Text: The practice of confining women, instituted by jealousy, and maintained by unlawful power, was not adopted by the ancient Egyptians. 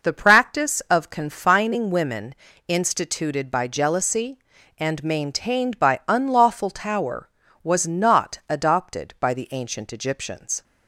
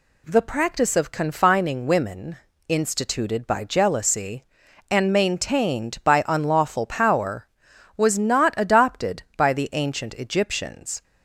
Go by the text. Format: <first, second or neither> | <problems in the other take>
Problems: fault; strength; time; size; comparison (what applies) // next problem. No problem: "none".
second | says "tower" for "power"; at 6.7 s